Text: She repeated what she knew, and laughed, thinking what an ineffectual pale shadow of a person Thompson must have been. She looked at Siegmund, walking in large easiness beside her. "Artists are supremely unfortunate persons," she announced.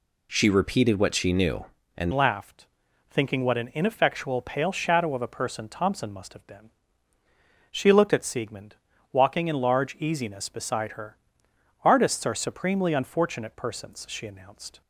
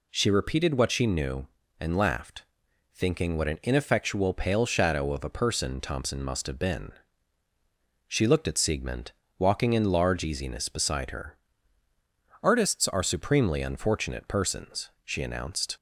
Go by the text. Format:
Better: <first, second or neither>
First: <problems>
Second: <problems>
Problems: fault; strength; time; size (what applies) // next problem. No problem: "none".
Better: second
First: changes voice at "laughed"; from 2.1 s on; 12.7 s long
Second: none